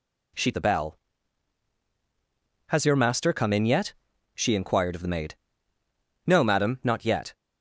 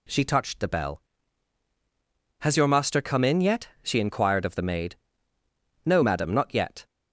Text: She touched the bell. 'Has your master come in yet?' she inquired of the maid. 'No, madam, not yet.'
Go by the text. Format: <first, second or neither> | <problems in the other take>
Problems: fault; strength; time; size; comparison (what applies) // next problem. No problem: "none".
second | skips "touched"; at 0.5 s